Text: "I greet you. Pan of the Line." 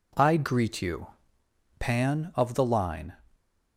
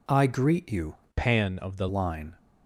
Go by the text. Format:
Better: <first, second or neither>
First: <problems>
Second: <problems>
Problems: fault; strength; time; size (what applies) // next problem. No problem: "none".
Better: first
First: none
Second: changes voice from "Pan" to "the"; from 1.1 to 1.8 s; 0.7 s long